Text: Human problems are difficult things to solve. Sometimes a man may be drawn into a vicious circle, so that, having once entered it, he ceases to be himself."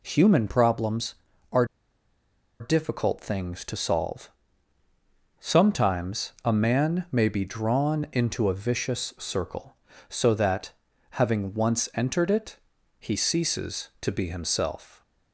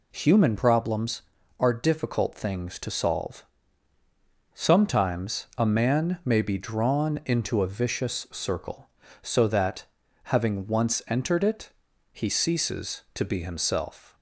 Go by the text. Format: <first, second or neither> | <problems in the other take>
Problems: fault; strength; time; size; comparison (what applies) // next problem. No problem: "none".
second | pauses between "are" and "difficult"; noticeable; at 1.6 s; 0.95 s long